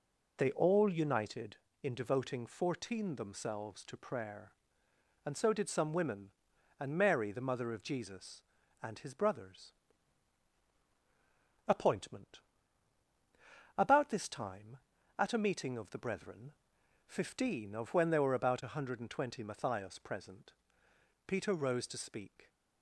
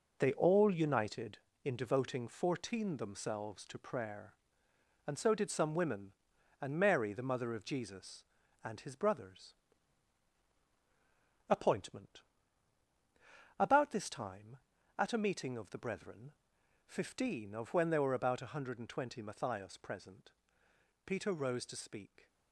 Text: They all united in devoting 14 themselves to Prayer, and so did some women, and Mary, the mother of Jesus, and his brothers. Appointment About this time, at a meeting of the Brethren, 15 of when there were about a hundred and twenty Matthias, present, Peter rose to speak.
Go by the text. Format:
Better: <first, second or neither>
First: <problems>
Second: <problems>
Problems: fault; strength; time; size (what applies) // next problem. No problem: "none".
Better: first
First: pauses between "Appointment" and "About"; strong; at 12.3 s; 1.3 s long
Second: gets quieter; strong; throughout; 7.5 dB // pauses between "Appointment" and "About"; strong; at 12.2 s; 1.3 s long